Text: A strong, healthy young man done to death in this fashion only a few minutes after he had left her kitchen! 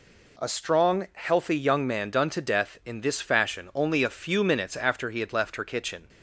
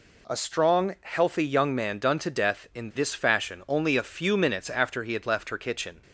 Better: neither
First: none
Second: none

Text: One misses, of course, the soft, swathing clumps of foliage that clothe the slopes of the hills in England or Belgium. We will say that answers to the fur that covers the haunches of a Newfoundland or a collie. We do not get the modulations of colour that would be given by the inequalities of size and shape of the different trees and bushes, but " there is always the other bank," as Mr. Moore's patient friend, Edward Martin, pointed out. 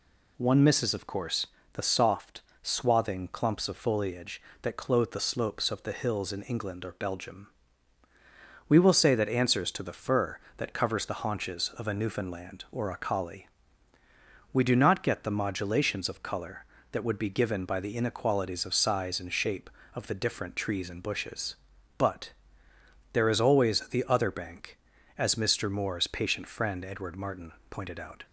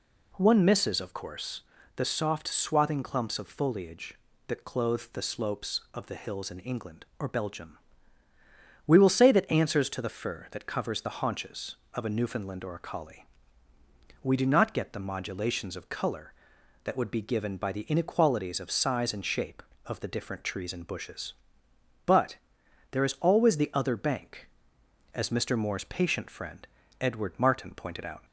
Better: neither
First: none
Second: none

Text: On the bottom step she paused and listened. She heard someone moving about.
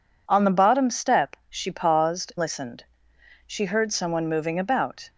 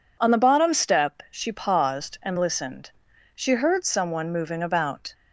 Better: second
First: skips "and"; at 2.3 s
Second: none

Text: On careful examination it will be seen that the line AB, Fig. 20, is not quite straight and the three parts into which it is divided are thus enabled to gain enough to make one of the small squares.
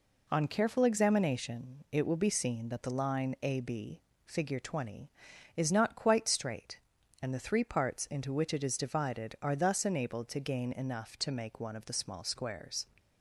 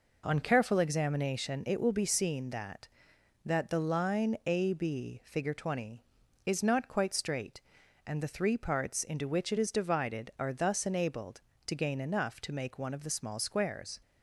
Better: first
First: none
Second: says "that" twice; at 3.4 s

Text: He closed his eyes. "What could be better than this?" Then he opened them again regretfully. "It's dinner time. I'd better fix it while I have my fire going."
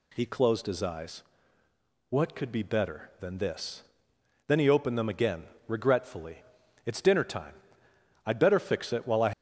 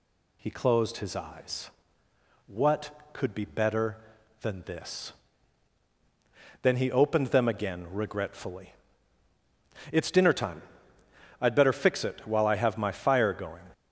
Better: second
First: pauses between "again" and "regretfully"; slight; at 5.4 s; 0.20 s long // stops before "have my fire going"; at 9.3 s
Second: none

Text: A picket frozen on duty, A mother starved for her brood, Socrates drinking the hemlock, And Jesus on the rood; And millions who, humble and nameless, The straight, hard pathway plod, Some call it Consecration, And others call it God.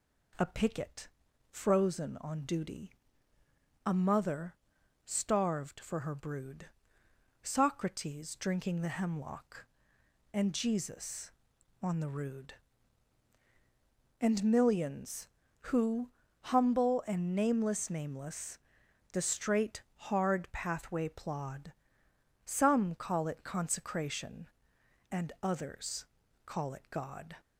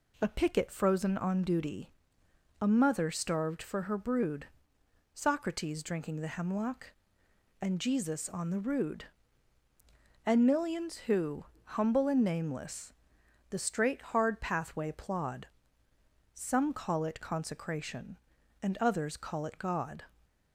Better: second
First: pauses between "picket" and "frozen"; at 1.0 s; 0.44 s long // pauses between "mother" and "starved"; noticeable; at 4.5 s; 0.50 s long // says "nameless" twice; at 17.8 s // pauses between "others" and "call"; at 26.0 s; 0.38 s long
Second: none

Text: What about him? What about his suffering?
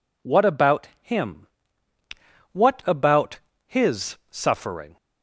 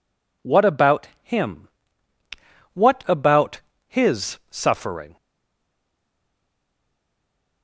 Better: first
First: pauses between "about" and "his"; slight; at 3.3 s; 0.28 s long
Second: pauses between "about" and "his"; slight; at 3.5 s; 0.28 s long // stays silent after the last word; from 5.1 s on; 2.5 s long

